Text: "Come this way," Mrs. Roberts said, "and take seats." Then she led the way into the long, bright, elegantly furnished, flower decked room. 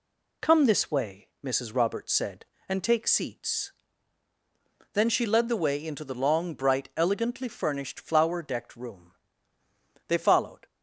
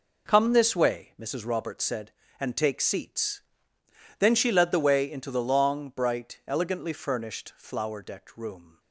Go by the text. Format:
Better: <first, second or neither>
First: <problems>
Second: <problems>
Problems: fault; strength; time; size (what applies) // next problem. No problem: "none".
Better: second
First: goes on to say "They followed"; from 10.0 s on; 0.58 s long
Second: none